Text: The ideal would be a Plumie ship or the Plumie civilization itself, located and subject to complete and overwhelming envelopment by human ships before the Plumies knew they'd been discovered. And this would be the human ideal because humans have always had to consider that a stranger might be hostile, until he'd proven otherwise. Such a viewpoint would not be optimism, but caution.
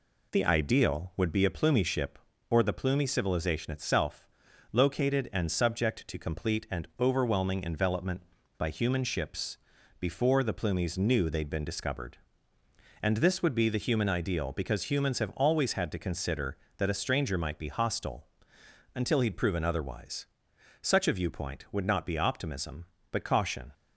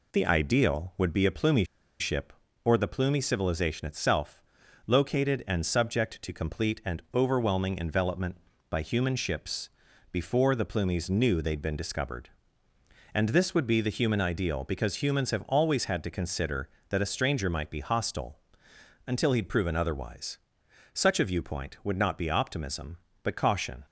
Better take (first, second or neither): first